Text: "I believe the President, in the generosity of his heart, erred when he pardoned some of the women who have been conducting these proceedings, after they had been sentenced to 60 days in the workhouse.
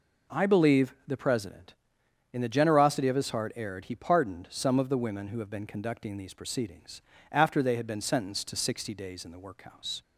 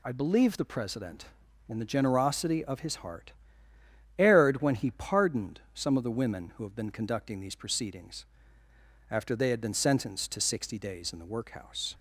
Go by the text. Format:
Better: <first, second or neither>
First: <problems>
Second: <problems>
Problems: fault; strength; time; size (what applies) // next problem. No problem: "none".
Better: second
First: skips "when"; at 3.8 s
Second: none